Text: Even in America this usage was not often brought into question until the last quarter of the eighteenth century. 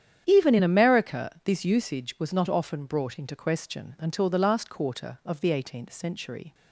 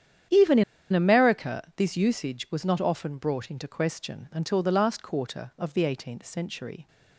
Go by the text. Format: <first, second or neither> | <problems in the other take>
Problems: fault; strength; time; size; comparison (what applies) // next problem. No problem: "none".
first | starts louder than the rest; strong; until 1.6 s; 9.5 dB; strong in the first // pauses between "in" and "America"; slight; at 0.6 s; 0.29 s long